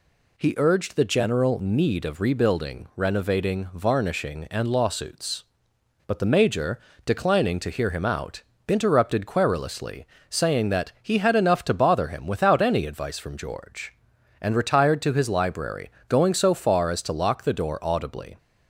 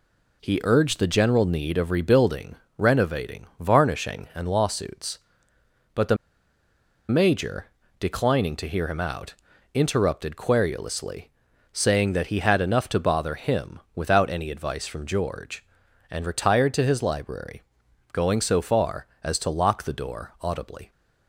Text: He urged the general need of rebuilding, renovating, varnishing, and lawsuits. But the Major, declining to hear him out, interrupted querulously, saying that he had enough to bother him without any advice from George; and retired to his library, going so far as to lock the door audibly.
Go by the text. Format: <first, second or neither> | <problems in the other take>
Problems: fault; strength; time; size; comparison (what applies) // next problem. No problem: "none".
first | pauses between "the" and "Major"; noticeable; at 6.1 s; 0.94 s long // pauses between "him" and "without"; slight; at 13.7 s; 0.16 s long